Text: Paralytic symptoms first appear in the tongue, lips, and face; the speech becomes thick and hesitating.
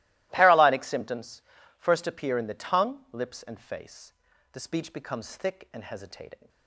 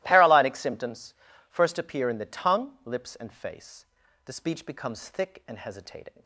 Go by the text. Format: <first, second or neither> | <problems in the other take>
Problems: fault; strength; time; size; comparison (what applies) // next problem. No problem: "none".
neither | starts louder than the rest; strong; the same in both // pauses between "symptoms" and "first"; the same in both